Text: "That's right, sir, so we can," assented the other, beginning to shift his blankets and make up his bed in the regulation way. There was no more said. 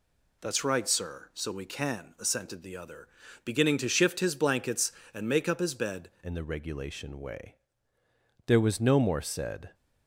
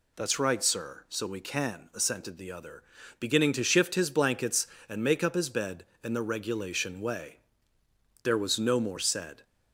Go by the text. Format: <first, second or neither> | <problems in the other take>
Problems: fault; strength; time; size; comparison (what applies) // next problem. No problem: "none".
second | changes voice at "in"; from 6.2 s on; 3.5 s long